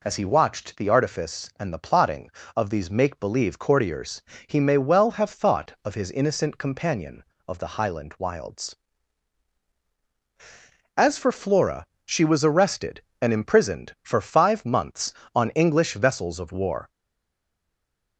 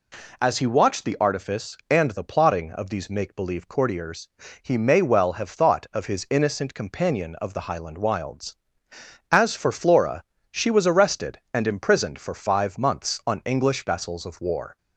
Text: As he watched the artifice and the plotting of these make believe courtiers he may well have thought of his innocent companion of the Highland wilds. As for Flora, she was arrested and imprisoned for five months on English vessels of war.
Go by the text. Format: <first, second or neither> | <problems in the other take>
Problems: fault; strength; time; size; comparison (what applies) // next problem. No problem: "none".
second | pauses between "courtiers" and "he"; slight; at 4.2 s; 0.28 s long; slight in the second // stays silent after the last word; noticeable; from 16.8 s on; 1.3 s long